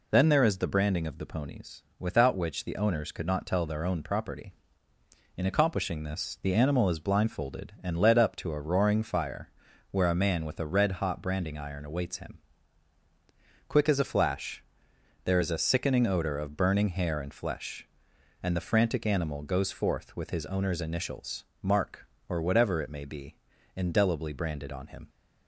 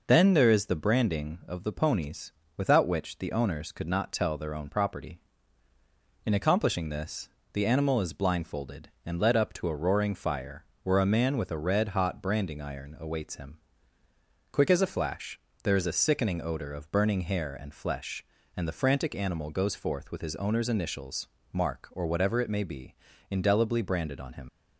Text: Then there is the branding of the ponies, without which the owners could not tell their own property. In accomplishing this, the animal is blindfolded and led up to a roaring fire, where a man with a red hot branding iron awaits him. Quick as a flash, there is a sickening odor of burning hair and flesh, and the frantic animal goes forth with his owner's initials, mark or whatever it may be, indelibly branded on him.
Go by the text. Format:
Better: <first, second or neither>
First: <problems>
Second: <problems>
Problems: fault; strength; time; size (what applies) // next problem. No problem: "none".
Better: first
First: none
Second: leaves "him" unfinished; at 24.4 s; 55 ms